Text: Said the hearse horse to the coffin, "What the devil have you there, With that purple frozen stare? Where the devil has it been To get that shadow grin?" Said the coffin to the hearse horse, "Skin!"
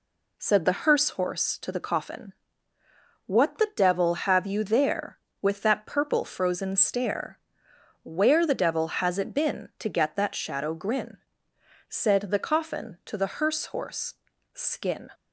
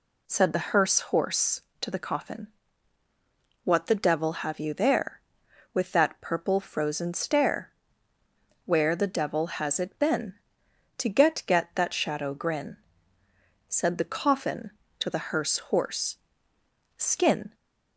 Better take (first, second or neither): first